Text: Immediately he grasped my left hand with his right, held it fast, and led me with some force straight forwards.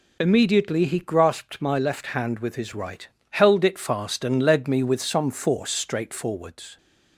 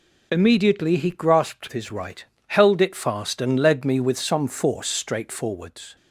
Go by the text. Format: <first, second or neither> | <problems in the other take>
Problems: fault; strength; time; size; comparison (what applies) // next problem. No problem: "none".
first | skips "my left hand with"; at 1.7 s